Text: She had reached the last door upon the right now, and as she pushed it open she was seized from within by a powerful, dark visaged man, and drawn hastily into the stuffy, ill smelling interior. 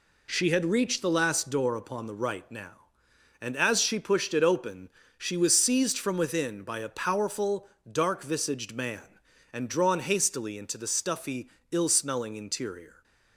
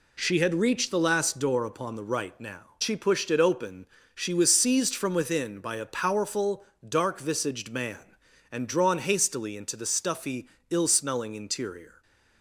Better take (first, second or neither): first